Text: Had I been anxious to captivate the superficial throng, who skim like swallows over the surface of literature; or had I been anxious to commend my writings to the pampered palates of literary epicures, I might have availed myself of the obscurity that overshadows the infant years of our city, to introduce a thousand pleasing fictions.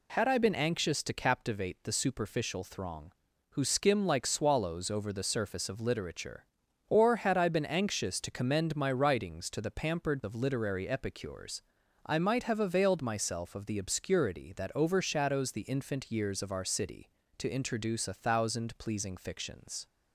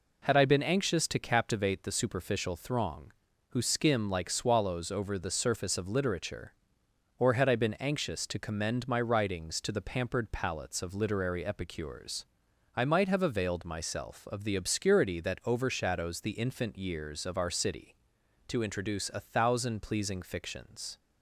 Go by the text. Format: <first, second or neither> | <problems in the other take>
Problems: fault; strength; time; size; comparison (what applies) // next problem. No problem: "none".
second | skips "palates"; at 10.2 s